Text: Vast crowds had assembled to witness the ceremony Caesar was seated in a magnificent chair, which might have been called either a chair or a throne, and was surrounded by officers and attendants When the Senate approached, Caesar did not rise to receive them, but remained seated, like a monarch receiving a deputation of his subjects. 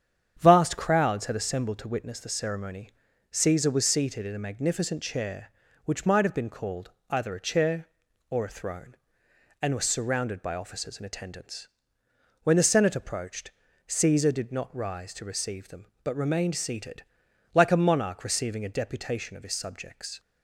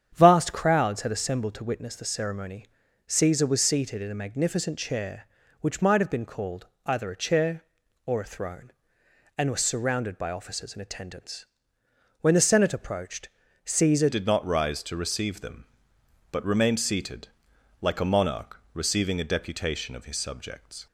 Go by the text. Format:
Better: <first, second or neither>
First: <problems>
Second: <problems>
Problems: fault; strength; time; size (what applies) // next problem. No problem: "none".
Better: first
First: starts louder than the rest; strong; until 1.4 s; 8.5 dB // pauses between "ceremony" and "Caesar"; at 2.8 s; 0.42 s long // pauses between "called" and "either"; slight; at 6.9 s; 0.18 s long // pauses between "attendants" and "When"; noticeable; at 11.6 s; 0.76 s long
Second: starts louder than the rest; strong; until 1.1 s; 8.5 dB // pauses between "ceremony" and "Caesar"; at 2.6 s; 0.42 s long // pauses between "called" and "either"; slight; at 6.6 s; 0.18 s long // pauses between "attendants" and "When"; noticeable; at 11.4 s; 0.76 s long // changes voice at "did"; from 14.0 s on; 6.8 s long